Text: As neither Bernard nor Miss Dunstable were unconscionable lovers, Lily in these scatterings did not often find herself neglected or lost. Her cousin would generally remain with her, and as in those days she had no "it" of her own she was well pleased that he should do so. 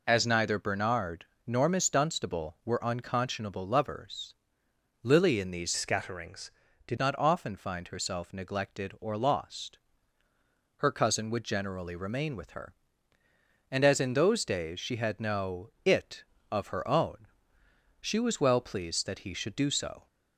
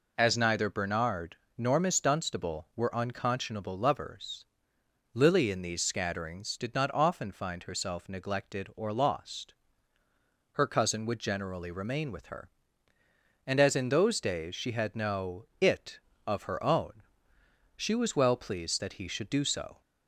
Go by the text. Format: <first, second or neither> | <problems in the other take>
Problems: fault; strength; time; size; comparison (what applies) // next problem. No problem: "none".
second | pauses between "Bernard" and "nor"; slight; at 1.2 s; 0.22 s long; slight in the second // changes voice from "scatterings" to "did"; from 5.7 to 6.9 s; 1.2 s long // pauses between "own" and "she"; noticeable; at 17.2 s; 0.74 s long; noticeable in the second